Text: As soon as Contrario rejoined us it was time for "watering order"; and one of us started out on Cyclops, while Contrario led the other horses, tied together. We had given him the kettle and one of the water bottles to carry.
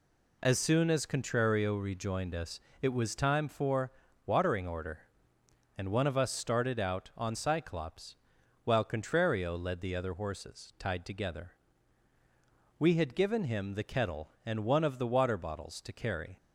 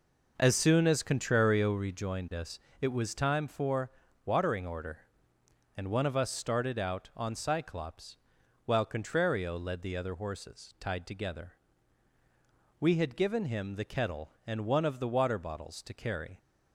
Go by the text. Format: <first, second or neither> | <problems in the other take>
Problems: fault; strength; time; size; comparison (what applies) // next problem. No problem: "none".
first | starts louder than the rest; noticeable; until 2.0 s; 5 dB // pauses between "us" and "it"; slight; at 2.5 s; 0.20 s long; slight in the first // pauses between "for" and "watering"; slight; at 3.8 s; 0.34 s long; slight in the first